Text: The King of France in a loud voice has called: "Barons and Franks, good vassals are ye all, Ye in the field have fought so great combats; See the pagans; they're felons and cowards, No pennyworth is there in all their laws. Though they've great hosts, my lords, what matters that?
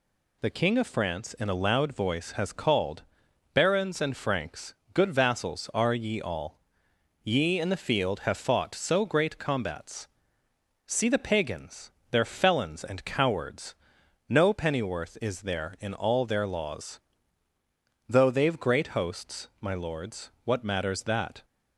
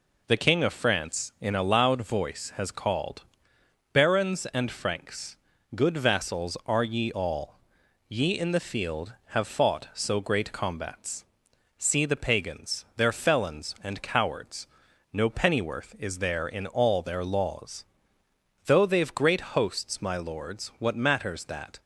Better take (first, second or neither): neither